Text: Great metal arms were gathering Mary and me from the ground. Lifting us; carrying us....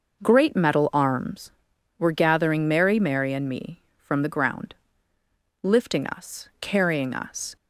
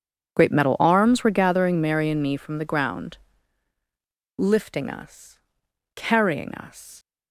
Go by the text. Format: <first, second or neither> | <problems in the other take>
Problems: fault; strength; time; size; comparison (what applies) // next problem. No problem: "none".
second | says "Mary" twice; at 2.9 s